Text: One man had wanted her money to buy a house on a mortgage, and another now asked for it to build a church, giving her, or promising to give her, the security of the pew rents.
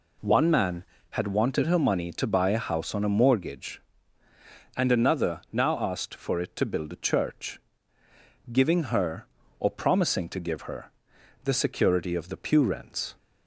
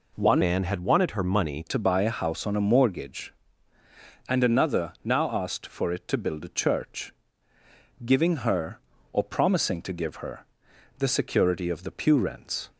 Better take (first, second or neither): first